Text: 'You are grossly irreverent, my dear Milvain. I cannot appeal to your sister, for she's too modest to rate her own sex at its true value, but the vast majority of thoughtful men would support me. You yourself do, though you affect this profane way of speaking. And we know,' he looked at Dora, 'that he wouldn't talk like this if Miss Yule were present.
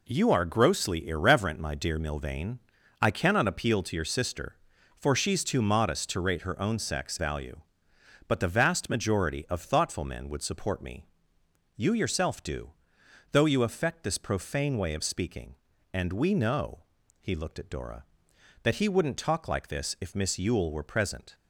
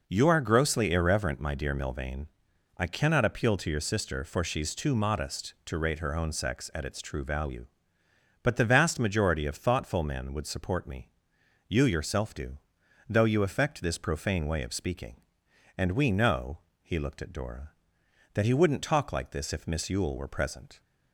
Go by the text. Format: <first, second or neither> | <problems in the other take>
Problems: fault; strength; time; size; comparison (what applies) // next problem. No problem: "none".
second | skips "at its true"; at 7.1 s